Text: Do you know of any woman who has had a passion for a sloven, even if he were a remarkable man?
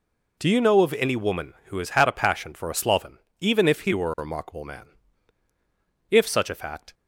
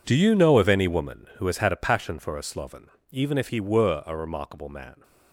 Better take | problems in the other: second | goes on to say "If such a fact"; noticeable; from 6.0 s on; 0.84 s long

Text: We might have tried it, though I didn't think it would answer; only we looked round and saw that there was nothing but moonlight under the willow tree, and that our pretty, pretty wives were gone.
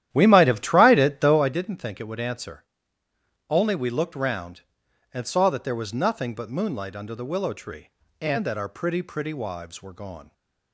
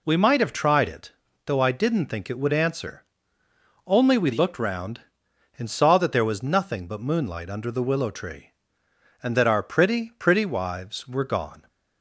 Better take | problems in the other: second | starts louder than the rest; strong; until 1.6 s; 11.5 dB

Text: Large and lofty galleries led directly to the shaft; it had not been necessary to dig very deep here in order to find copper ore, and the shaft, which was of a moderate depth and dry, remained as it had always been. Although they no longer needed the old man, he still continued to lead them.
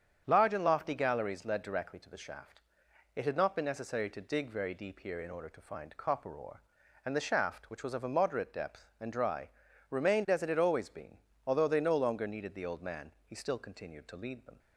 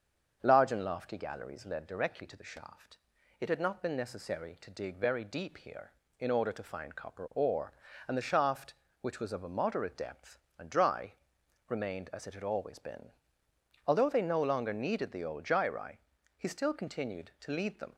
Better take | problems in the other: first | starts louder than the rest; until 1.4 s; 7 dB; strong in the first // says "gyri" for "man"; at 15.4 s

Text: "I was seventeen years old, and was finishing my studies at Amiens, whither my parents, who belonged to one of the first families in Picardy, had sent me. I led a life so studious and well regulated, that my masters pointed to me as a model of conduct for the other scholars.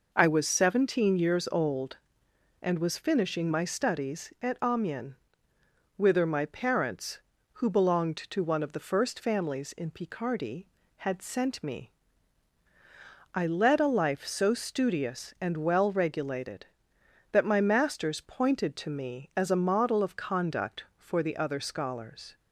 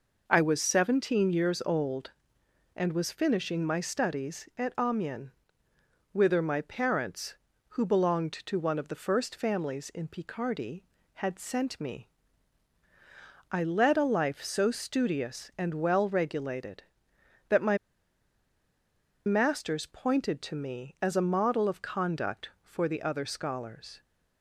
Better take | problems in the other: first | pauses between "my" and "masters"; strong; at 17.7 s; 1.4 s long

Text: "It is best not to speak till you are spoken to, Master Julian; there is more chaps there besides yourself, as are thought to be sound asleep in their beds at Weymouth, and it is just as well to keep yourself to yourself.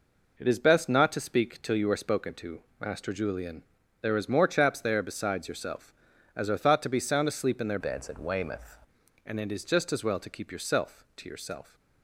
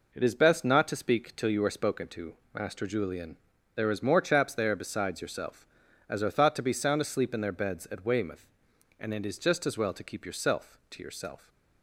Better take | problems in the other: second | changes voice from "beds" to "Weymouth"; from 7.7 to 8.7 s; 1.0 s long

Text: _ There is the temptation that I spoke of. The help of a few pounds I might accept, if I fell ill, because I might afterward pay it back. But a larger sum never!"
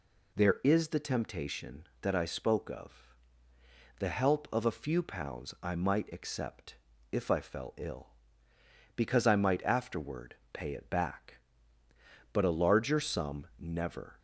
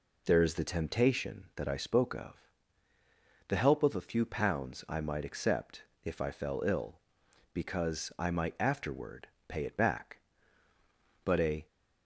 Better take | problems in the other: first | pauses between "afterward" and "pay"; slight; at 9.2 s; 0.22 s long; slight in the first // stops before "larger sum never"; at 11.6 s

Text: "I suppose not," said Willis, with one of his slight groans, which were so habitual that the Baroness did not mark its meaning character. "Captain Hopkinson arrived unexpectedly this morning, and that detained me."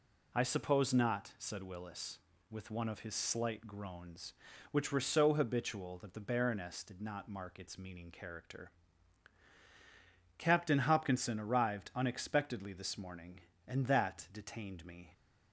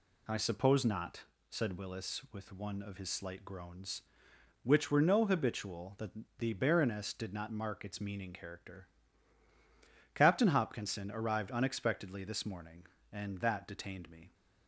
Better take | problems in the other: first | says "no" for "so"; at 5.0 s // pauses between "that" and "the"; slight; at 6.1 s; 0.28 s long

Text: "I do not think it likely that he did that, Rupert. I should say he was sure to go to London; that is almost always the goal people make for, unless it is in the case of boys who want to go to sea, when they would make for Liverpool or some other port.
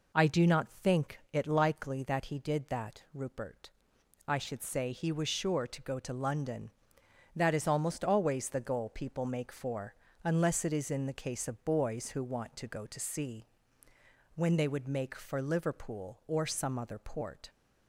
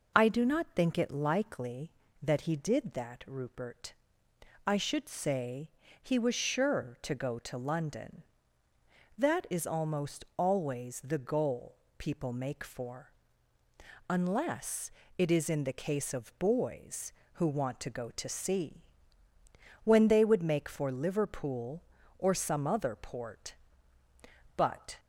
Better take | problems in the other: first | pauses between "say" and "he"; slight; at 5.6 s; 0.32 s long // pauses between "goal" and "people"; slight; at 11.7 s; 0.20 s long // pauses between "unless" and "it"; slight; at 14.9 s; 0.26 s long // goes on to say "But"; slight; from 24.5 s on; 0.42 s long

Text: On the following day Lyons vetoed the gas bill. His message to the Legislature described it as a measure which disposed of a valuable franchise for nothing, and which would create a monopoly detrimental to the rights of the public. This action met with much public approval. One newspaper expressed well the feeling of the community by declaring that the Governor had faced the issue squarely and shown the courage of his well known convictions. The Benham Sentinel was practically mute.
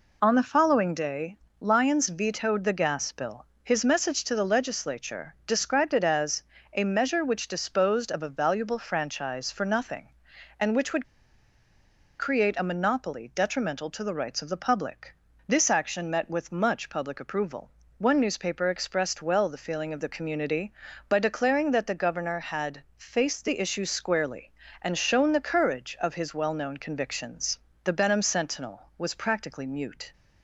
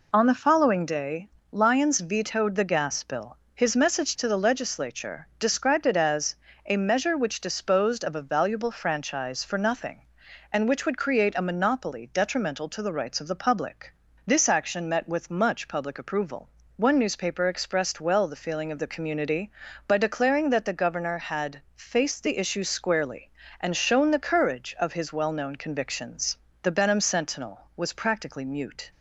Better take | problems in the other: second | pauses between "day" and "Lyons"; slight; at 1.3 s; 0.24 s long; slight in the second // pauses between "as" and "a"; slight; at 6.4 s; 0.32 s long; slight in the second // pauses between "would" and "create"; at 11.0 s; 1.1 s long // pauses between "had" and "faced"; slight; at 22.8 s; 0.16 s long; slight in the second

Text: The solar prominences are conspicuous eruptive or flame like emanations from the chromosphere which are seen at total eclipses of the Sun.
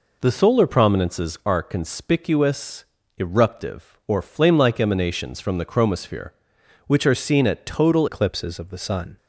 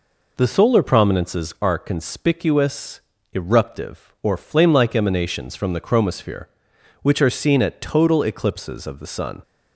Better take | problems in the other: second | pauses between "conspicuous" and "eruptive"; slight; at 2.8 s; 0.32 s long; slight in the second // changes voice at "eclipses"; from 8.0 s on; 1.1 s long

